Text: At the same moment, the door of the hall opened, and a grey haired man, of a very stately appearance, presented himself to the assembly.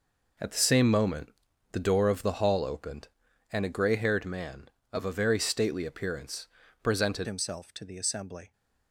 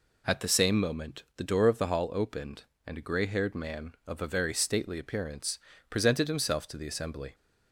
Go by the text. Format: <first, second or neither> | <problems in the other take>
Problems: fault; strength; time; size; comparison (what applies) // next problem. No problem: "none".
second | changes voice at "himself"; from 7.2 s on; 1.3 s long